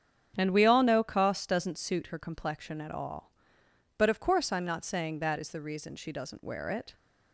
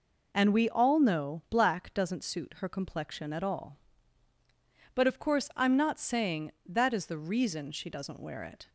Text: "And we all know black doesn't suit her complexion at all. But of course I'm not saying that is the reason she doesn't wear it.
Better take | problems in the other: second | starts louder than the rest; strong; until 1.3 s; 8 dB // says "koss" for "black"; at 1.0 s

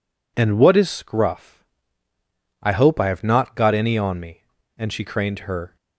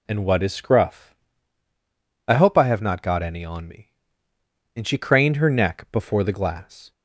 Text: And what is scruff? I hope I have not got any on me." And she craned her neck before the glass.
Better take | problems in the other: second | stops before "neck before the glass"; at 5.7 s

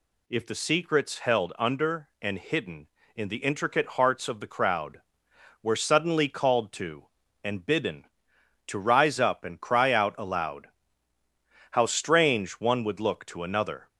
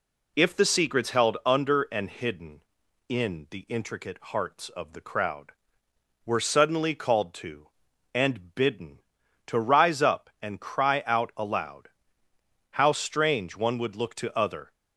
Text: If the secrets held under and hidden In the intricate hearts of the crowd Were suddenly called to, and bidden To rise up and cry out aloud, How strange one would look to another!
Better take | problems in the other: first | says "other" for "another"; at 14.3 s

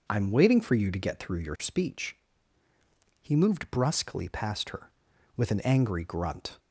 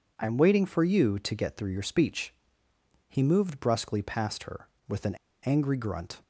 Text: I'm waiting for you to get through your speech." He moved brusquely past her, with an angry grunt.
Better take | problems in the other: first | pauses between "an" and "angry"; slight; at 5.1 s; 0.27 s long

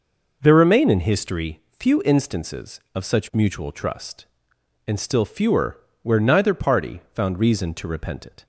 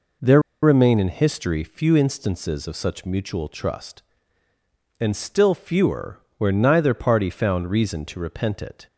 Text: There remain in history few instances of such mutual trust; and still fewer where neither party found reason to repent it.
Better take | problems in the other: first | pauses between "There" and "remain"; slight; at 0.4 s; 0.21 s long // pauses between "fewer" and "where"; slight; at 6.1 s; 0.20 s long; slight in the first

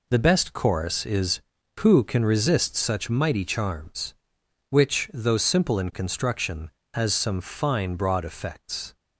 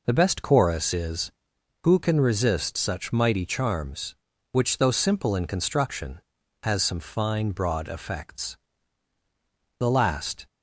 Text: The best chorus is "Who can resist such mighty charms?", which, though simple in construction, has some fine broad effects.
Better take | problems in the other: first | goes on to say "The last"; noticeable; from 9.7 s on; 0.68 s long

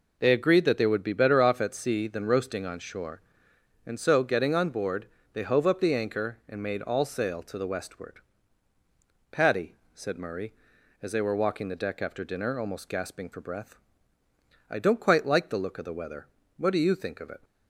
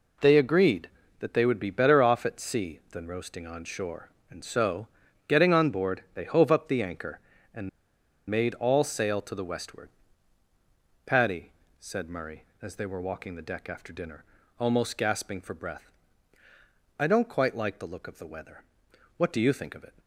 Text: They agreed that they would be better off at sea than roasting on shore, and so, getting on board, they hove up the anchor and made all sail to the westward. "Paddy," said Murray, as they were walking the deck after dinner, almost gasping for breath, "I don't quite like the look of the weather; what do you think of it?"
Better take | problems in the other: first | pauses between "and" and "made"; noticeable; at 7.6 s; 0.60 s long

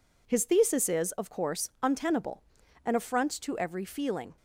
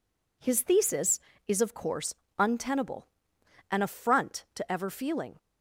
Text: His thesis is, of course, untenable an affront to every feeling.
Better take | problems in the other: first | pauses between "untenable" and "an"; noticeable; at 3.0 s; 0.66 s long; also in the first // says "ever" for "every"; at 4.7 s

